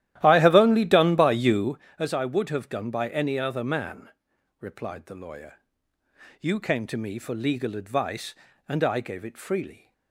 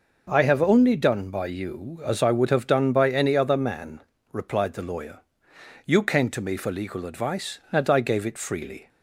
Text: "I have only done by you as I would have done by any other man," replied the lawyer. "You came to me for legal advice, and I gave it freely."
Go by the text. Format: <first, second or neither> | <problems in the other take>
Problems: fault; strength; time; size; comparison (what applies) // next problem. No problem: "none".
second | starts louder than the rest; strong; until 1.8 s; 13.5 dB